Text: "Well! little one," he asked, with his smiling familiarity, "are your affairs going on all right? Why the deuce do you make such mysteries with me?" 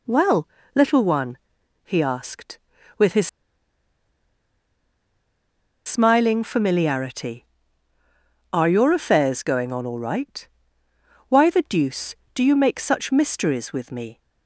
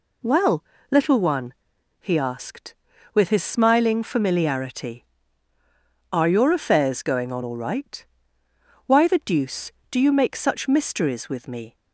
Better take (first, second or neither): second